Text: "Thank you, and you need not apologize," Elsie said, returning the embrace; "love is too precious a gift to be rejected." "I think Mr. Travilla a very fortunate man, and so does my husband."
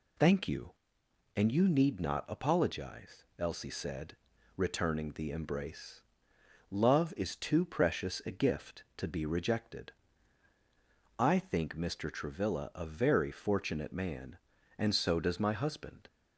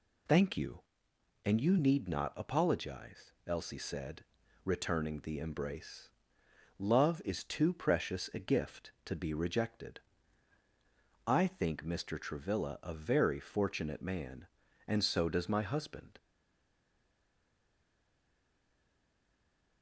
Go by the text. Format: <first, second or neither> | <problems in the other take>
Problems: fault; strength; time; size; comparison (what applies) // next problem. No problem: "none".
first | stays silent after the last word; strong; from 16.1 s on; 3.7 s long